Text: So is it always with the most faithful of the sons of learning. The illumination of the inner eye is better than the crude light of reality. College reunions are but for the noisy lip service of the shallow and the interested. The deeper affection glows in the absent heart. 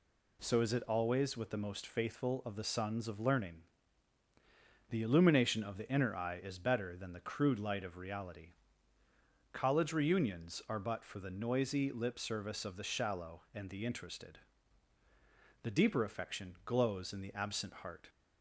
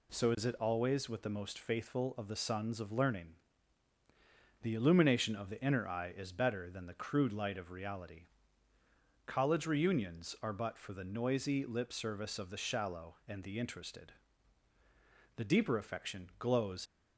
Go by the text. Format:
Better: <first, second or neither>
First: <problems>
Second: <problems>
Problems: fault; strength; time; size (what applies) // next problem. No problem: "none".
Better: first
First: none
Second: stops before "in the absent heart"; at 16.8 s